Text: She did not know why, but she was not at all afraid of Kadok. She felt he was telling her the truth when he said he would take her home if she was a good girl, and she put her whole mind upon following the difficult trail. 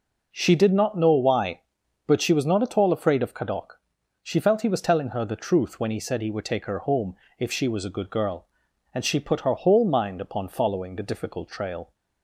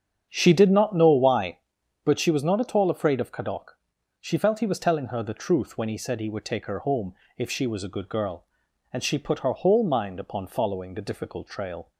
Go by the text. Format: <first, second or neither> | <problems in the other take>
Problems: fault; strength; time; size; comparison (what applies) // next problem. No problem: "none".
first | starts louder than the rest; strong; until 1.5 s; 8 dB // pauses between "home" and "if"; slight; at 7.1 s; 0.22 s long; slight in the first